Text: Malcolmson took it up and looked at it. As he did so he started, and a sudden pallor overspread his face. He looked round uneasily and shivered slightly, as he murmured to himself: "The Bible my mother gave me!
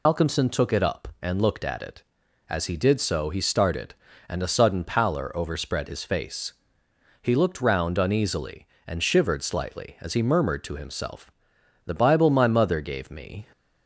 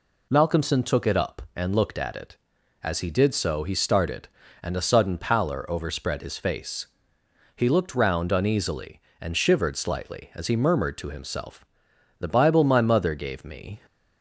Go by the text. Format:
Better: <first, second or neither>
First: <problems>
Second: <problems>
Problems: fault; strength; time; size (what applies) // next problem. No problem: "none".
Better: second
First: loses the start of "Malcolmson"; at 0.0 s; 85 ms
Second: none